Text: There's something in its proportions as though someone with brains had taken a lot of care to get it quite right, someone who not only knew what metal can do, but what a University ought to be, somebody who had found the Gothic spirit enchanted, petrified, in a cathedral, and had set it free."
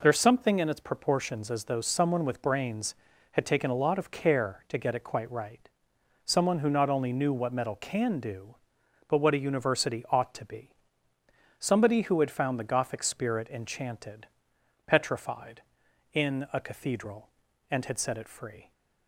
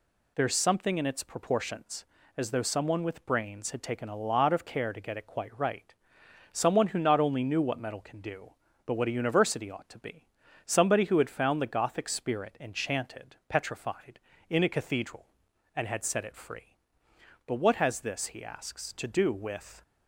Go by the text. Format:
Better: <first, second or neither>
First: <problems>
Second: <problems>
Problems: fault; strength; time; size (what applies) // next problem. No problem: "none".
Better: first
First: none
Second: goes on to say "But what has this he asks to do with"; strong; from 17.4 s on; 2.3 s long